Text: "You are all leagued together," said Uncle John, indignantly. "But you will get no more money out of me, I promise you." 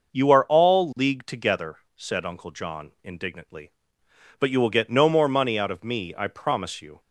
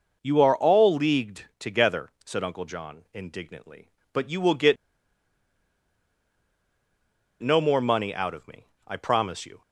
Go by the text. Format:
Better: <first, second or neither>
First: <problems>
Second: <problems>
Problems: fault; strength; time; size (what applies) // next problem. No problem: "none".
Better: first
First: none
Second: pauses between "get" and "no"; strong; at 4.7 s; 2.6 s long